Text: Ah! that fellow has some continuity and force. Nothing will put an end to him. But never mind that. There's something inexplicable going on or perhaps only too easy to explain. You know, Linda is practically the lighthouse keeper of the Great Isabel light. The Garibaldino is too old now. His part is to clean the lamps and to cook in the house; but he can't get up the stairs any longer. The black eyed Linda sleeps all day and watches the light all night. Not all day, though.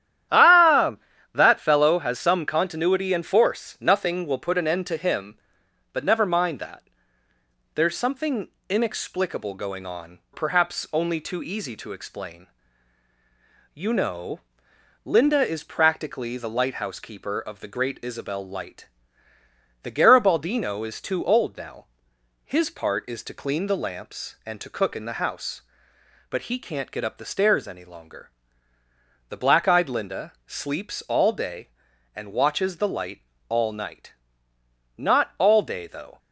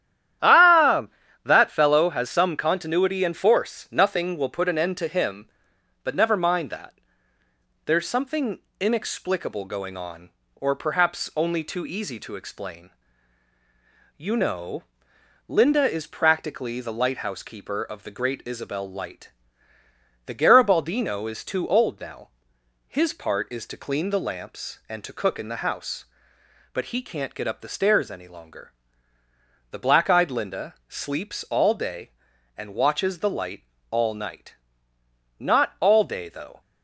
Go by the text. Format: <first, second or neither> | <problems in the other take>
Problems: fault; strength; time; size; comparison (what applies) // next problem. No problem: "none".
second | starts louder than the rest; strong; until 1.6 s; 11 dB; strong in the second // pauses between "something" and "inexplicable"; slight; at 8.4 s; 0.20 s long; slight in the second // skips "or"; at 10.2 s // pauses between "light" and "all"; slight; at 33.2 s; 0.26 s long; slight in the second